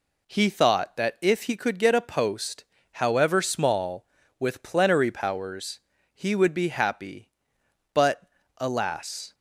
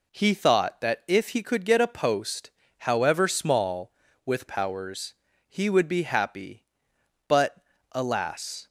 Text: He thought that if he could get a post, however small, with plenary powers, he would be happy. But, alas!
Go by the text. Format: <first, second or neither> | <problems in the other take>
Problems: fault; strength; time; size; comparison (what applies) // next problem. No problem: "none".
first | skips "plenary"; at 4.4 s